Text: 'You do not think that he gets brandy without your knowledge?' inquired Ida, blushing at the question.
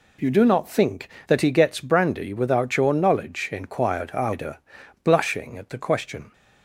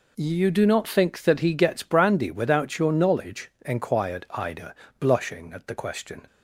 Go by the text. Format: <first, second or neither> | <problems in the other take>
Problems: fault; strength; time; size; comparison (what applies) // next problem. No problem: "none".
neither | none